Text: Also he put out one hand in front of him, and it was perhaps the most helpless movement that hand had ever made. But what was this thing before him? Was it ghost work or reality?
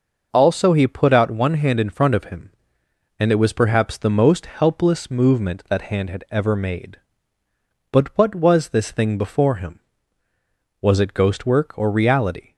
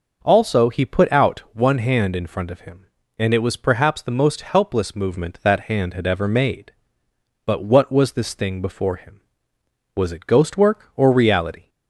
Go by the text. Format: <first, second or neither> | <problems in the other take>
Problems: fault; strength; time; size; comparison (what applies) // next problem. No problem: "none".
neither | none